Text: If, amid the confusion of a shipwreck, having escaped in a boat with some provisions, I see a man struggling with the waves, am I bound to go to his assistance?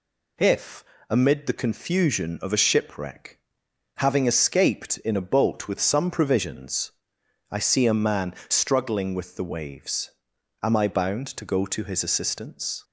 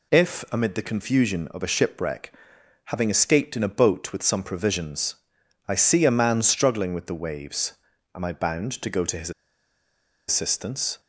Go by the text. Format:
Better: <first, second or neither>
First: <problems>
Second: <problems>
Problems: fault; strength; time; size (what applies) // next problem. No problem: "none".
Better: first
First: none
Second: pauses between "his" and "assistance"; noticeable; at 9.3 s; 0.97 s long